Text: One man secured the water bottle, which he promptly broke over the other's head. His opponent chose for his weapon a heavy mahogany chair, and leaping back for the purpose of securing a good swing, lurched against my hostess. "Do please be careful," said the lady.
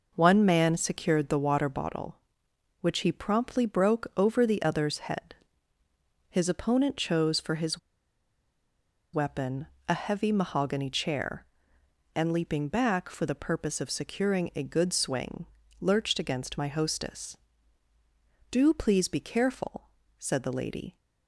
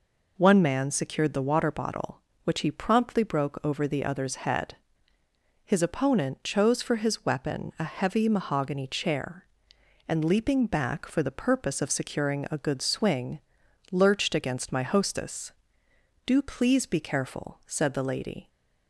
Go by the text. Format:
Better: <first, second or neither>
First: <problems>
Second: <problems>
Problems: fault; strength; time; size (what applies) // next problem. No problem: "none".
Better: second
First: pauses between "his" and "weapon"; strong; at 7.7 s; 1.3 s long // pauses between "weapon" and "a"; slight; at 9.6 s; 0.20 s long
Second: none